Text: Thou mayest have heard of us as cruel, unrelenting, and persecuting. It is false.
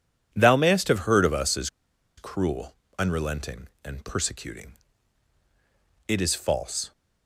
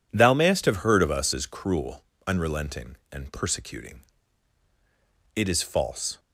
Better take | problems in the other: second | pauses between "as" and "cruel"; noticeable; at 1.6 s; 0.49 s long

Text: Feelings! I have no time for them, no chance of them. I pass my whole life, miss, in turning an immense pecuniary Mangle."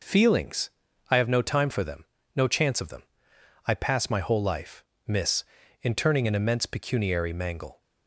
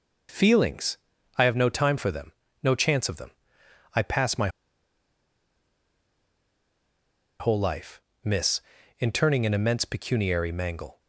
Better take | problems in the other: first | pauses between "my" and "whole"; strong; at 4.4 s; 2.9 s long

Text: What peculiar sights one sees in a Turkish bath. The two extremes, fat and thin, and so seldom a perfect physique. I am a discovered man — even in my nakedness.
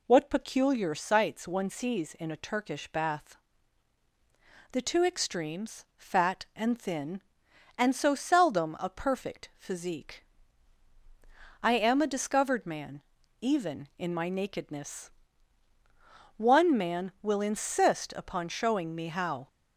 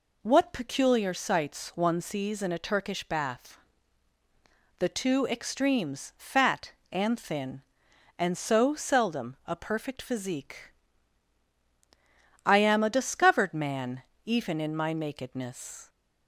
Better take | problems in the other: second | goes on to say "One man will insist upon showing me how"; strong; from 16.3 s on; 3.1 s long

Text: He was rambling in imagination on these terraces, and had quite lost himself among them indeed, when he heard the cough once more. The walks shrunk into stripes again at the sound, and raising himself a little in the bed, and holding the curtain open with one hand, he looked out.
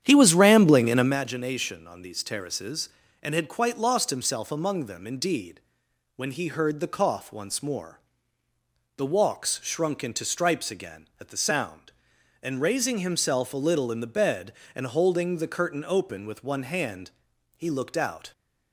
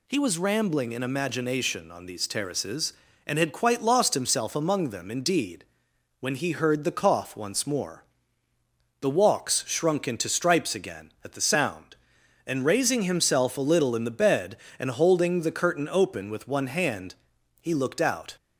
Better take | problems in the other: second | starts louder than the rest; strong; until 1.2 s; 9.5 dB

